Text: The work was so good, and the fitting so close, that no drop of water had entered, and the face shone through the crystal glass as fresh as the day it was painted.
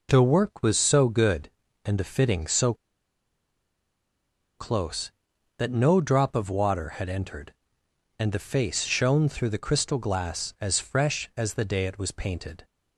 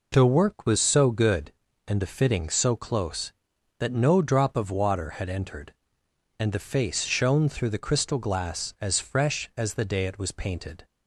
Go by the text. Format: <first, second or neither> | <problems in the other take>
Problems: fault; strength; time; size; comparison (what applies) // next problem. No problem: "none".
second | pauses between "so" and "close"; strong; at 2.7 s; 1.8 s long